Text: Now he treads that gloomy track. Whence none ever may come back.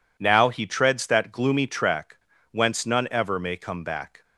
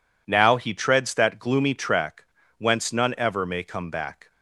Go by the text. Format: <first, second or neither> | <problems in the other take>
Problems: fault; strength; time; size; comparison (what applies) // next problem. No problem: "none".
neither | none